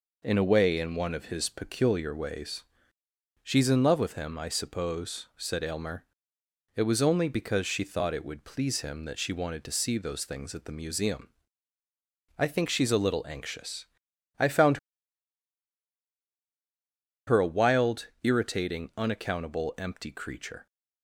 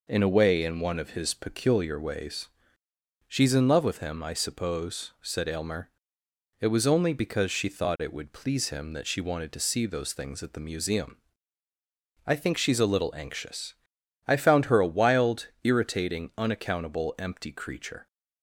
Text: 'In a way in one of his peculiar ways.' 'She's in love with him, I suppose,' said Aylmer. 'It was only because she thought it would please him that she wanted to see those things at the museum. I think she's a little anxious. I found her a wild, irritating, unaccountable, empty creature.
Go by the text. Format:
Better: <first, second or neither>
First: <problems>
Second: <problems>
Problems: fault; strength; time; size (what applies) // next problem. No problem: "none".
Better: second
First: pauses between "found" and "her"; strong; at 14.7 s; 2.4 s long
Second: none